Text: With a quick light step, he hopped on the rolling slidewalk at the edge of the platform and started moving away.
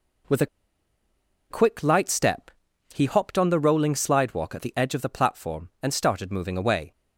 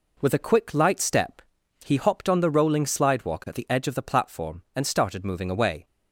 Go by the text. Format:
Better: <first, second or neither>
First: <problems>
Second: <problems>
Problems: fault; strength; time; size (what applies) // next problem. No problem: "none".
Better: second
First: pauses between "a" and "quick"; at 0.4 s; 1.0 s long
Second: none